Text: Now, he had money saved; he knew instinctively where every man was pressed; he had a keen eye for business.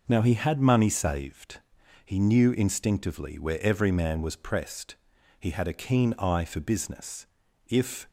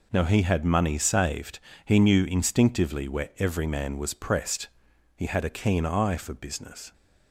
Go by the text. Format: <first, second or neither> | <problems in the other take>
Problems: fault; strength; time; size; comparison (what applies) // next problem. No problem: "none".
second | goes on to say "If"; slight; from 7.6 s on; 0.40 s long